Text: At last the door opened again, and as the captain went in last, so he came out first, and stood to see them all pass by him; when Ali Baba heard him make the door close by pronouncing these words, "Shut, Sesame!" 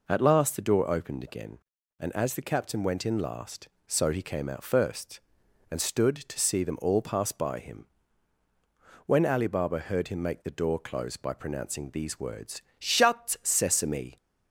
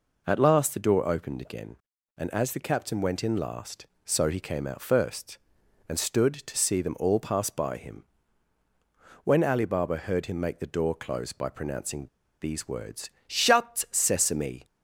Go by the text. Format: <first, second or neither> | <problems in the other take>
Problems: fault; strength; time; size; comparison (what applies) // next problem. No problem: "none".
first | pauses between "pronouncing" and "these"; slight; at 12.0 s; 0.35 s long